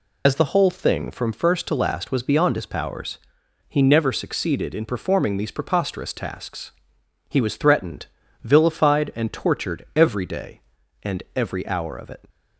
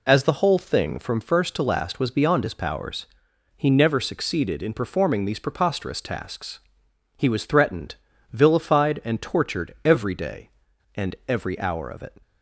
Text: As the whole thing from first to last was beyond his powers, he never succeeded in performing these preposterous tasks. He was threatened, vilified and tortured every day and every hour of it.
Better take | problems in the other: second | loses the start of "As"; at 0.2 s; 65 ms

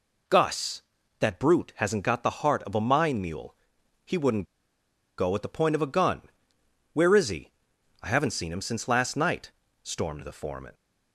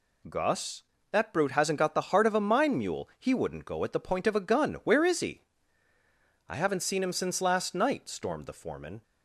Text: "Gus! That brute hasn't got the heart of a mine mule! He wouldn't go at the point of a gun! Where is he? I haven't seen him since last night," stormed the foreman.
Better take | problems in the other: second | pauses between "wouldn't" and "go"; noticeable; at 4.4 s; 0.74 s long

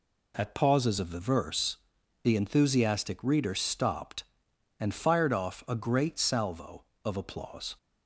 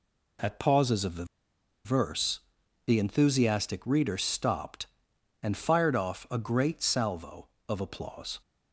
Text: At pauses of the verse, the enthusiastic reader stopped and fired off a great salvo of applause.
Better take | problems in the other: first | pauses between "the" and "verse"; noticeable; at 1.2 s; 0.59 s long

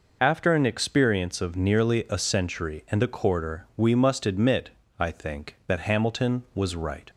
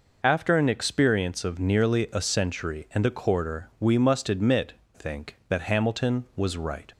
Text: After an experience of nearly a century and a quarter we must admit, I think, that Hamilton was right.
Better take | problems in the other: first | skips "I"; at 4.8 s

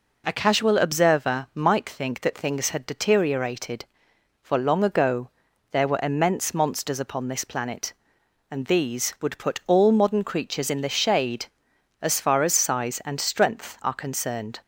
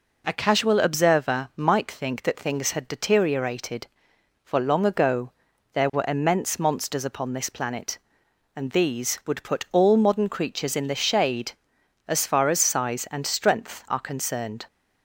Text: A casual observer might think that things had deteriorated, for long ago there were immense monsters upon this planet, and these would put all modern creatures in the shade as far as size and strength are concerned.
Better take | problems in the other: neither | pauses between "ago" and "there"; the same in both

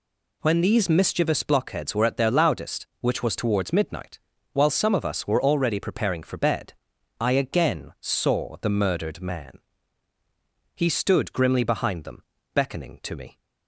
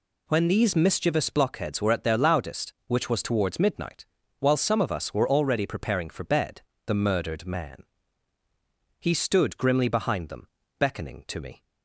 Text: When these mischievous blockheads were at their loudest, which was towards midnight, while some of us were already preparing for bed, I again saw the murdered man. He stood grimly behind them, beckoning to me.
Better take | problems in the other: first | skips "I again saw"; at 6.7 s

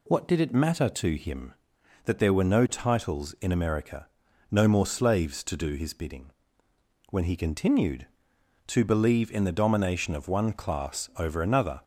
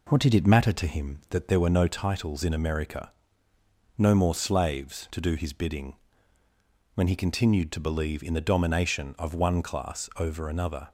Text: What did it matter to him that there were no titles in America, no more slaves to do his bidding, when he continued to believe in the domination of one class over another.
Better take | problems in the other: first | starts louder than the rest; until 1.3 s; 3.5 dB

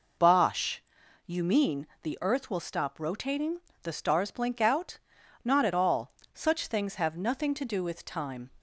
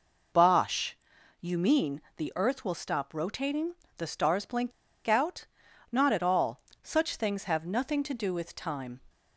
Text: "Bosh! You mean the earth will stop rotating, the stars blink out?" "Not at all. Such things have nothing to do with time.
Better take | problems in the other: first | pauses between "mean" and "the"; slight; at 2.0 s; 0.16 s long; slight in the first // pauses between "blink" and "out"; slight; at 4.7 s; 0.34 s long

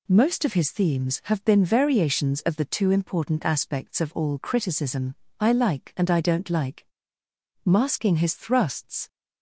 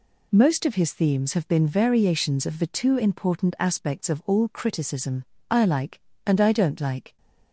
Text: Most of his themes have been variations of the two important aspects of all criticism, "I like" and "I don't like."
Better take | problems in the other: second | goes on to say "Masking his thrusts"; from 7.6 s on; 1.4 s long

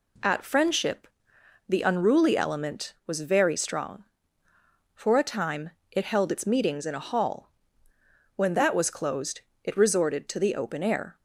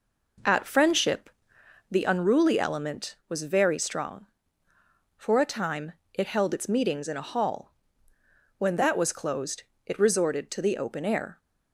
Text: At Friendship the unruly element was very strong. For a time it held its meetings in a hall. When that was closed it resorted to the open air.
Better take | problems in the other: first | starts louder than the rest; noticeable; until 2.0 s; 5 dB // pauses between "Friendship" and "the"; noticeable; at 1.2 s; 0.62 s long; noticeable in the first // pauses between "time" and "it"; slight; at 5.9 s; 0.20 s long; slight in the first // pauses between "closed" and "it"; slight; at 9.6 s; 0.22 s long; slight in the first

